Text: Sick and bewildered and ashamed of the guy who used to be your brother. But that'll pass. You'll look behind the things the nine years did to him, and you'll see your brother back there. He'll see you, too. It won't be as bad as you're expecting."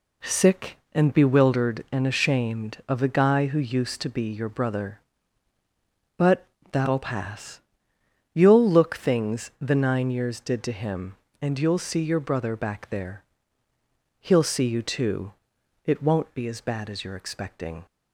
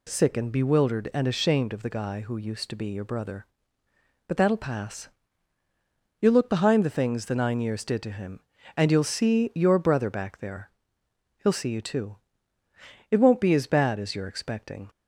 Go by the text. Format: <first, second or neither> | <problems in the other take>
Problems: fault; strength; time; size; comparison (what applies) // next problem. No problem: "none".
second | pauses between "But" and "that'll"; slight; at 6.4 s; 0.24 s long // skips "behind the"; at 8.9 s